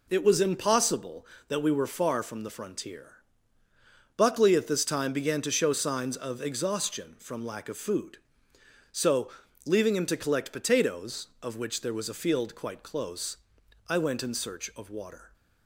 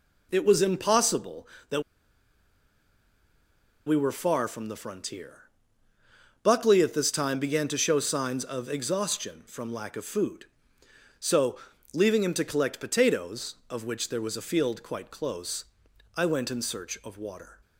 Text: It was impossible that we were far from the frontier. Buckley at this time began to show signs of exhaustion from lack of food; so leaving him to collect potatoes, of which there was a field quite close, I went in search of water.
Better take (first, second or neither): first